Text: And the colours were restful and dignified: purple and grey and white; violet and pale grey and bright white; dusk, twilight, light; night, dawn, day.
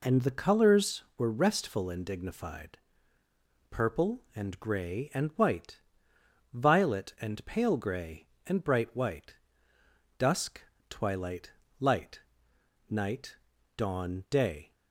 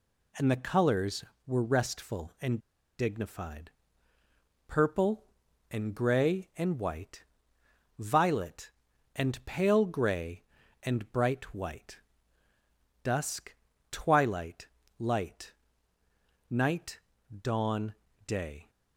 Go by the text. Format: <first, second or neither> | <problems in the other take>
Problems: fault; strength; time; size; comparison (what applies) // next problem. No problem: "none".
first | pauses between "and" and "dignified"; at 2.5 s; 0.39 s long